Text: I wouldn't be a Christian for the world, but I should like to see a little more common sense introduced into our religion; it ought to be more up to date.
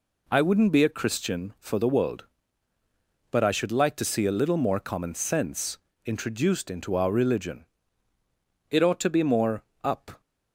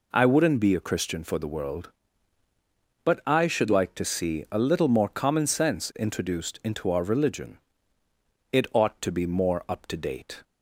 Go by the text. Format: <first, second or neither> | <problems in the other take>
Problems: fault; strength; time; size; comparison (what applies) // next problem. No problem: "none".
second | pauses between "sense" and "introduced"; slight; at 5.7 s; 0.27 s long // pauses between "more" and "up"; slight; at 9.6 s; 0.22 s long // stops before "to date"; at 10.2 s